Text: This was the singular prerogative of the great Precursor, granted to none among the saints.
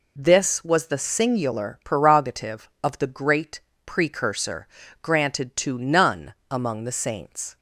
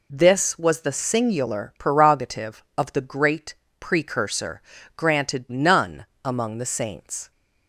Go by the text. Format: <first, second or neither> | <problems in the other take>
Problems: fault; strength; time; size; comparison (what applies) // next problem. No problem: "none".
first | pauses between "great" and "Precursor"; slight; at 3.5 s; 0.24 s long; slight in the first // skips "to"; at 5.4 s // pauses between "none" and "among"; slight; at 6.0 s; 0.18 s long; slight in the first